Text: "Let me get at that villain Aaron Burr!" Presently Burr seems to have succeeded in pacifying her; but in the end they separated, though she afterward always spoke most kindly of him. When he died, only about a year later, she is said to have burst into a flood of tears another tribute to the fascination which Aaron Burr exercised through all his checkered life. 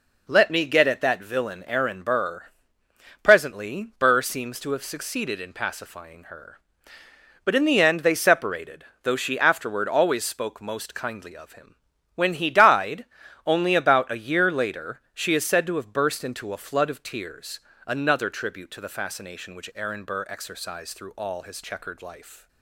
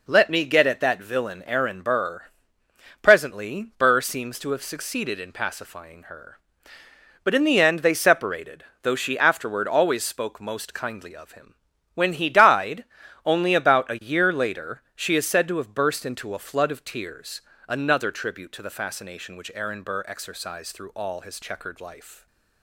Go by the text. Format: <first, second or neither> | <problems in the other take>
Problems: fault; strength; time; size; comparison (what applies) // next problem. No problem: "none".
neither | pauses between "tears" and "another"; slight; the same in both